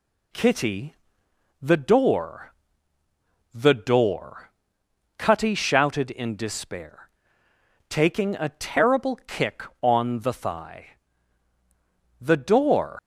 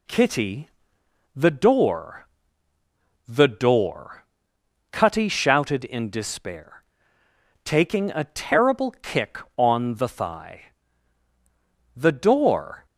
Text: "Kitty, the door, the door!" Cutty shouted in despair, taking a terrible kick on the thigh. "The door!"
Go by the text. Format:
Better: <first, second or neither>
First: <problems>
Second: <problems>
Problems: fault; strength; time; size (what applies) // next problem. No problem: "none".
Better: second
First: leaves "door" unfinished; at 12.9 s; 110 ms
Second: none